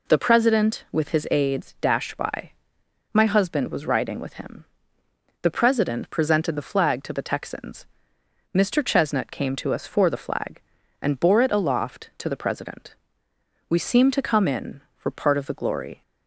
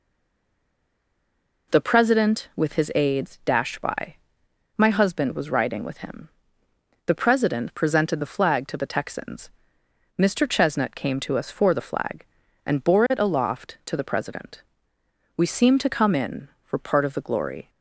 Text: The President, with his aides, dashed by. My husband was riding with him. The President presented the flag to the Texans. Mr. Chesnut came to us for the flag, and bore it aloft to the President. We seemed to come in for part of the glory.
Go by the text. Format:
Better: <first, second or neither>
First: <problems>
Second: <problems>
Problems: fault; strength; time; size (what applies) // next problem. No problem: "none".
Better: first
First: none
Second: stays silent before the first word; noticeable; until 1.6 s; 1.6 s long